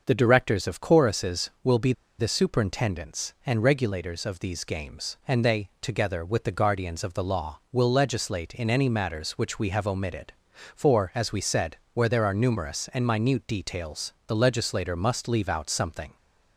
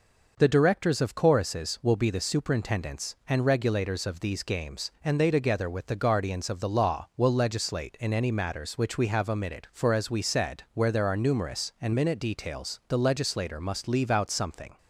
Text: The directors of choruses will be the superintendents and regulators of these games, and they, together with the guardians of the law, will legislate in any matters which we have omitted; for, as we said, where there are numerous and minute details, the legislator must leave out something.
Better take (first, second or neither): second